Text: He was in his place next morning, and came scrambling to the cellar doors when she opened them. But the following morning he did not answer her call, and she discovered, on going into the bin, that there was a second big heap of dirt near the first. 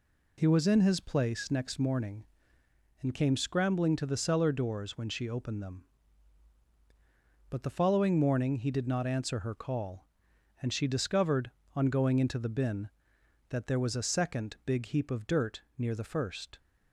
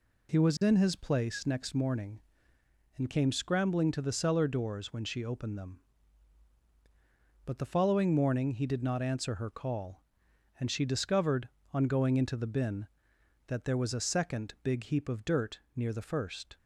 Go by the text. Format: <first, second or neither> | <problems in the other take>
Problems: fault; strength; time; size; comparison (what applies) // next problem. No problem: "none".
neither | pauses between "dirt" and "near"; slight; the same in both